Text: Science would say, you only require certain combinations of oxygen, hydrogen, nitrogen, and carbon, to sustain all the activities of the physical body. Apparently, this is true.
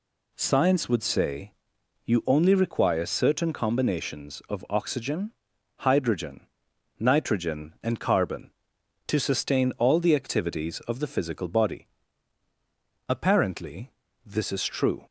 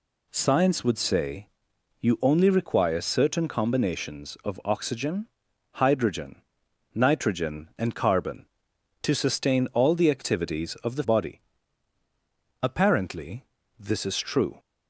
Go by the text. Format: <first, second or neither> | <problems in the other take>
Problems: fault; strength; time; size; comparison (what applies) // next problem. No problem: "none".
first | skips "physical"; at 11.0 s